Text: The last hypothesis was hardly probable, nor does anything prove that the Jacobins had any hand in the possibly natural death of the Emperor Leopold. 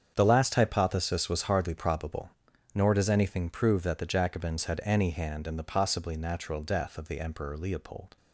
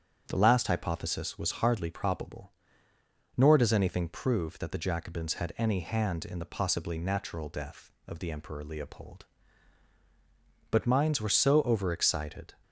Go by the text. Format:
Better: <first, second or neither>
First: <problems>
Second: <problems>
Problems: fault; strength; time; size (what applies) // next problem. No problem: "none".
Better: first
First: starts louder than the rest; strong; until 1.1 s; 7.5 dB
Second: starts louder than the rest; strong; until 1.2 s; 8 dB // goes on to say "But minds were so overexcited"; strong; from 10.6 s on; 1.8 s long